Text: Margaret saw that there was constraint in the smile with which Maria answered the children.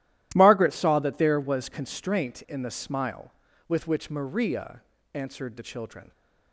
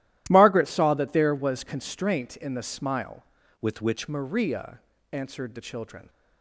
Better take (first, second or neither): first